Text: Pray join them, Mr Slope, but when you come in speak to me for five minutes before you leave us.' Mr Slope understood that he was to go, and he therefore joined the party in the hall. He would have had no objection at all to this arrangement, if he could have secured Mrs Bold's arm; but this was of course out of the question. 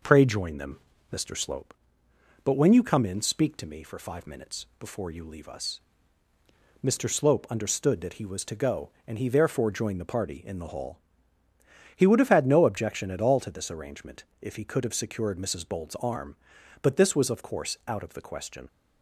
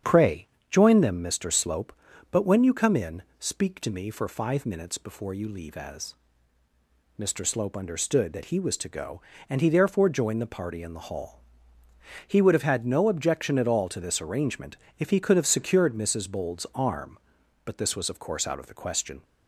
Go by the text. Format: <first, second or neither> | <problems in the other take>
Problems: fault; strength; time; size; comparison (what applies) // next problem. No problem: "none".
first | starts louder than the rest; strong; until 1.2 s; 8 dB // pauses between "Pray" and "join"; slight; at 0.4 s; 0.22 s long // pauses between "in" and "speak"; slight; at 3.2 s; 0.16 s long // says "as" for "us"; at 5.7 s